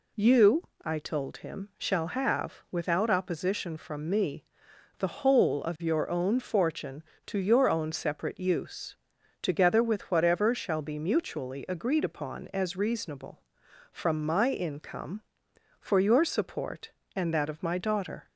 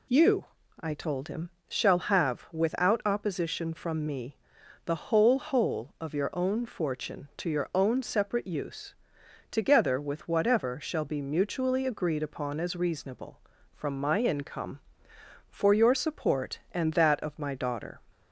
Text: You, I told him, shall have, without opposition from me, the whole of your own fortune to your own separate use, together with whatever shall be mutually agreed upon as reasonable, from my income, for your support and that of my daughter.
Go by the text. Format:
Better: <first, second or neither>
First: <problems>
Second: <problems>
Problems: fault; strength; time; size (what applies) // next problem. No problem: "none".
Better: first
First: none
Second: says "whole" twice; at 5.3 s